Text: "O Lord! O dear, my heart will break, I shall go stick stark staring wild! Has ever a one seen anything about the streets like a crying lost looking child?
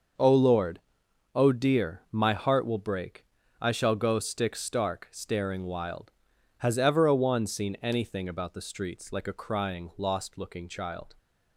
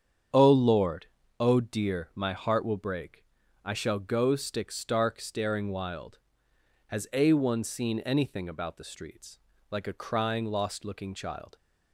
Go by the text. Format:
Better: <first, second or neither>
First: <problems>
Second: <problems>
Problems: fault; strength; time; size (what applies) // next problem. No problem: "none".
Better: first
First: starts louder than the rest; noticeable; until 1.7 s; 6 dB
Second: starts louder than the rest; strong; until 1.6 s; 8 dB // skips "ever"; at 7.1 s // pauses between "streets" and "like"; slight; at 9.3 s; 0.32 s long